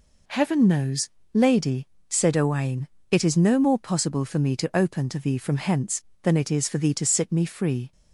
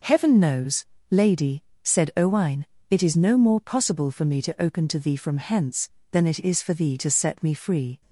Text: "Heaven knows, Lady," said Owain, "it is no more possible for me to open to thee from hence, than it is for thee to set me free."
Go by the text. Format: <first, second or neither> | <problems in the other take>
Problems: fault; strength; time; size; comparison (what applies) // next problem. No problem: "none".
second | says "sit" for "set"; at 7.0 s